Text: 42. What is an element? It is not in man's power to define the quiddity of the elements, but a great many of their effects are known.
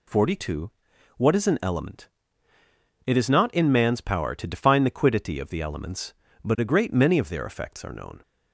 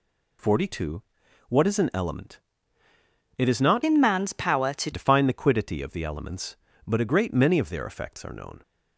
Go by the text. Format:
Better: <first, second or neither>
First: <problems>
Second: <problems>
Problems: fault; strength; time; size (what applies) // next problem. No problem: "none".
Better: first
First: none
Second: changes voice from "in" to "to"; from 3.8 to 4.9 s; 1.1 s long